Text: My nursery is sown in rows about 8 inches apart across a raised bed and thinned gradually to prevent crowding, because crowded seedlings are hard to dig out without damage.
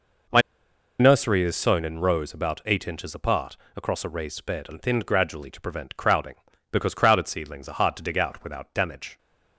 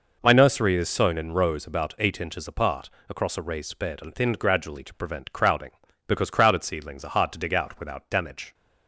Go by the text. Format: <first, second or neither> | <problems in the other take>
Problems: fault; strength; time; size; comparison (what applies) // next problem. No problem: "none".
second | pauses between "My" and "nursery"; noticeable; at 0.4 s; 0.58 s long // pauses between "apart" and "across"; slight; at 3.5 s; 0.20 s long; slight in the second